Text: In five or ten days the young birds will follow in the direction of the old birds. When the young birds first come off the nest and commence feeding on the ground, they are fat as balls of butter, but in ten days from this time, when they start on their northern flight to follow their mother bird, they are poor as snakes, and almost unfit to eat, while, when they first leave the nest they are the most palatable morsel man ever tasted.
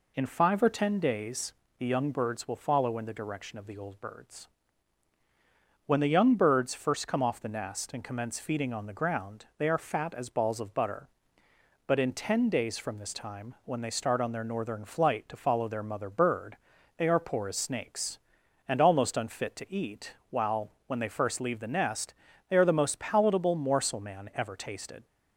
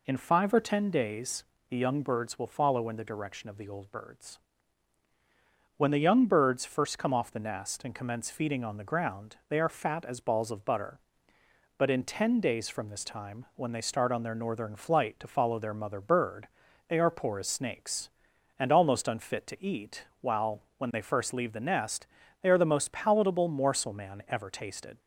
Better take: neither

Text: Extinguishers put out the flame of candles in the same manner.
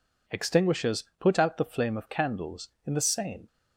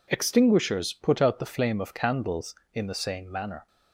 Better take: second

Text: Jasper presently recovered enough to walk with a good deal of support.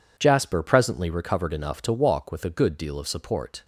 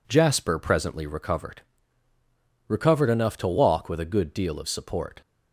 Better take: first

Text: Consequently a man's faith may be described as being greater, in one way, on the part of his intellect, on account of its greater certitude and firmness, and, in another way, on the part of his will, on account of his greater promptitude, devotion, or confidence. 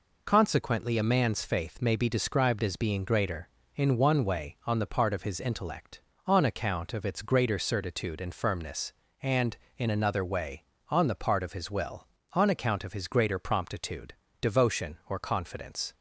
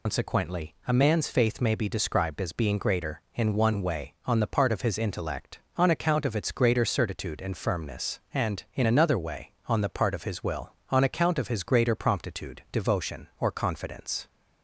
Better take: first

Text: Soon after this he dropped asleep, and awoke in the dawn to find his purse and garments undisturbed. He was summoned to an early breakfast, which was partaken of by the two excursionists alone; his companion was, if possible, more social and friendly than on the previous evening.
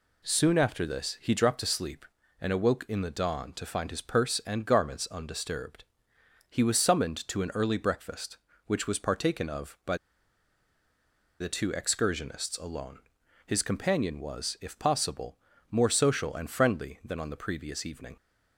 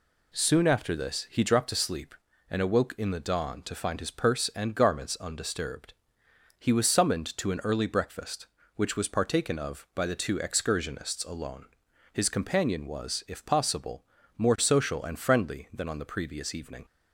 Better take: second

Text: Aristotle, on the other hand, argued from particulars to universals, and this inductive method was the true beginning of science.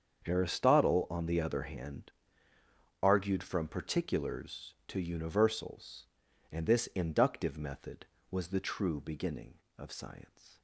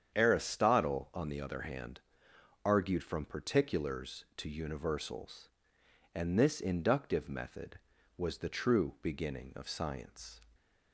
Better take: neither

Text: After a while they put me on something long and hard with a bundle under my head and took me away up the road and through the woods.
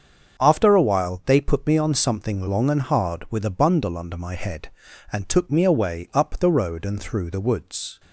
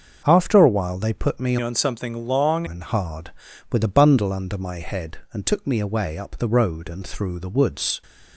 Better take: first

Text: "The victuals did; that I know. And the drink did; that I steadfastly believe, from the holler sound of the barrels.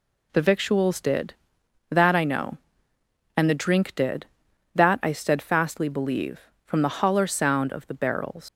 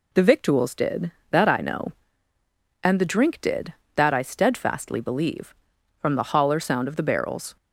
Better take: second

